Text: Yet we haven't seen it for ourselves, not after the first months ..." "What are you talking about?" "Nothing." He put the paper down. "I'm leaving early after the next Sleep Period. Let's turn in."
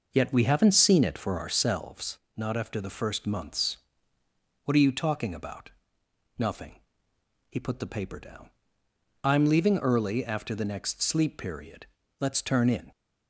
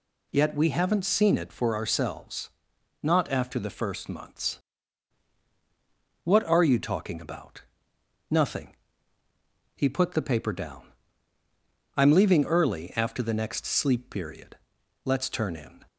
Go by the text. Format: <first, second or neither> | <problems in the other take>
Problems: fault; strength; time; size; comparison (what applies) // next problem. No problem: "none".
second | starts louder than the rest; noticeable; until 1.8 s; 5.5 dB